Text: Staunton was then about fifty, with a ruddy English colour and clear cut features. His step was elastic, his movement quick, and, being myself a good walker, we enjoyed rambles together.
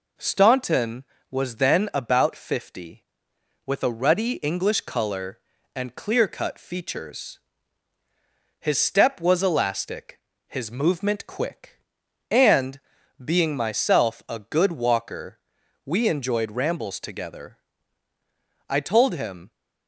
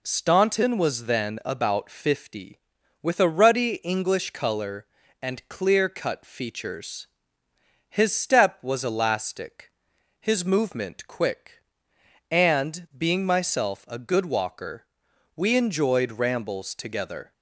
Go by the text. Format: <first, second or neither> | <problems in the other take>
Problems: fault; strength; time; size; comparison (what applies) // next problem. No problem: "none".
second | goes on to say "I told him"; noticeable; from 18.6 s on; 0.82 s long